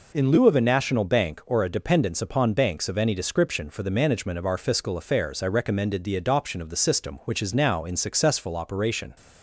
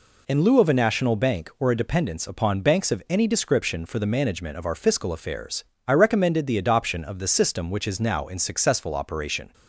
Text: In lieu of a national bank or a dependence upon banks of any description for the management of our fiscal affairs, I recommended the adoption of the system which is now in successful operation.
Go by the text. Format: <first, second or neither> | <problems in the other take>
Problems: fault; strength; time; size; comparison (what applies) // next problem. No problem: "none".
neither | none